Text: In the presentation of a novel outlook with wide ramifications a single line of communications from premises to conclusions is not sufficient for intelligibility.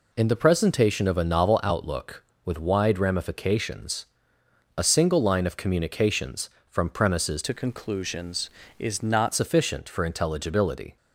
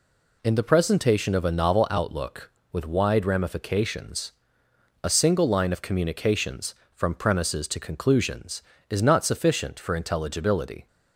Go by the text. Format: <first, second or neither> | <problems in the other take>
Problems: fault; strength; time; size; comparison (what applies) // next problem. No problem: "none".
second | pauses between "ramifications" and "a"; noticeable; at 4.0 s; 0.72 s long; noticeable in the second // changes voice from "to" to "not"; from 7.4 to 9.3 s; 1.9 s long